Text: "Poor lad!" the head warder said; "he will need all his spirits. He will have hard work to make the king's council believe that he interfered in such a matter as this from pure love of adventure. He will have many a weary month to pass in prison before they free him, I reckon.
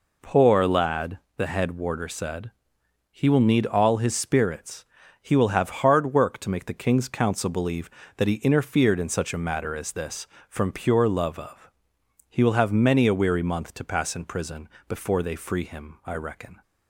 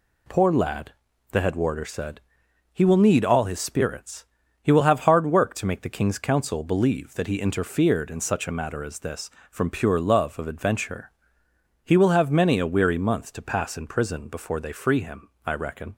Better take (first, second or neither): second